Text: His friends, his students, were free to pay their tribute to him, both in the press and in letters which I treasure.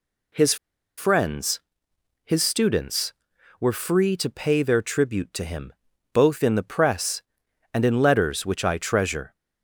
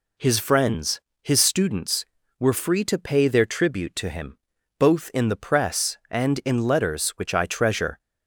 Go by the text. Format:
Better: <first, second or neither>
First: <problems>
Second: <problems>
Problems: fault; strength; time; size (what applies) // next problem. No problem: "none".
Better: second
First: pauses between "His" and "friends"; at 0.5 s; 0.42 s long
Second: none